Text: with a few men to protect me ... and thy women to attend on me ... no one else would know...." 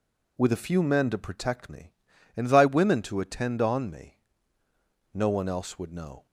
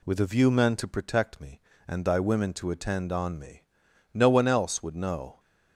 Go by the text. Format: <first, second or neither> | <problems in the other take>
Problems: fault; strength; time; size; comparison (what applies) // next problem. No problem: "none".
first | says "view" for "few"; at 0.2 s